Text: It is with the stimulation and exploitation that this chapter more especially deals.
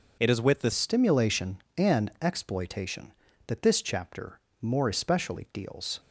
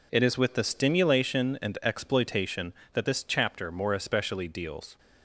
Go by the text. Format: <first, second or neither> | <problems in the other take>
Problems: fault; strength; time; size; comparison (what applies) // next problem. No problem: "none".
second | changes voice at "stimulation"; from 0.7 s on; 5.2 s long // pauses between "chapter" and "more"; slight; at 4.3 s; 0.20 s long